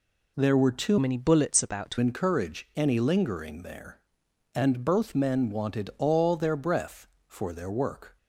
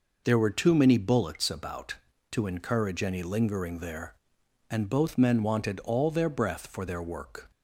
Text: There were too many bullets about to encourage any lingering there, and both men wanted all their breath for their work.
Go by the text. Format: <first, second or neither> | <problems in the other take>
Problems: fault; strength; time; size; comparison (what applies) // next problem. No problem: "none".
second | changes voice from "many" to "to"; from 0.9 to 1.9 s; 1.0 s long